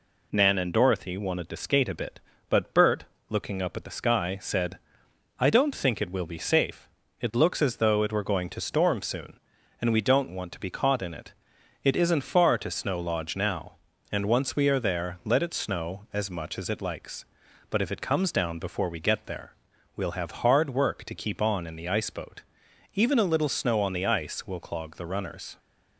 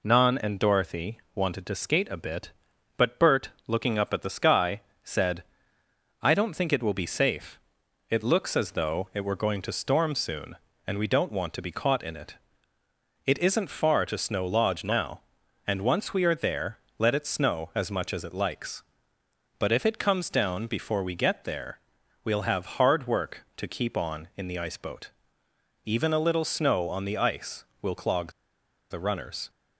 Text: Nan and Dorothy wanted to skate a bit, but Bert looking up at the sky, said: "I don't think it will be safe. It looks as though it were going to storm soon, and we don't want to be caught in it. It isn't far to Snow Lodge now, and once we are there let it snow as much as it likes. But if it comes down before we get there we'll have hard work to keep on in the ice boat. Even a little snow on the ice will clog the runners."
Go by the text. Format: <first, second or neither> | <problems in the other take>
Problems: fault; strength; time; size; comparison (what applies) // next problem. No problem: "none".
first | pauses between "Dorothy" and "wanted"; slight; at 1.1 s; 0.16 s long // pauses between "Bert" and "looking"; slight; at 3.4 s; 0.16 s long; slight in the first // pauses between "there" and "let"; slight; at 16.7 s; 0.22 s long // pauses between "there" and "we'll"; at 21.7 s; 0.44 s long; also in the first // pauses between "clog" and "the"; noticeable; at 28.3 s; 0.58 s long